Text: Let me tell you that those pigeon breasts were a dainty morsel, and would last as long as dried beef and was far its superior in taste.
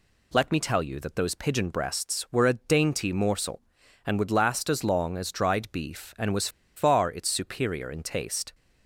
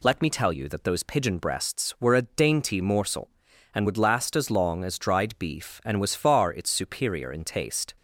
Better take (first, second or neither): second